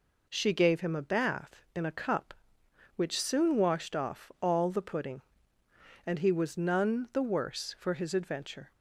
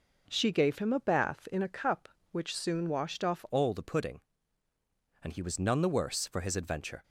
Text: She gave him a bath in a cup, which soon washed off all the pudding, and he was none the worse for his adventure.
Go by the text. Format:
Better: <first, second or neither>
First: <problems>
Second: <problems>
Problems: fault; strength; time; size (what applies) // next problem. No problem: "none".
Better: first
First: none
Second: changes voice at "all"; from 3.5 s on; 3.5 s long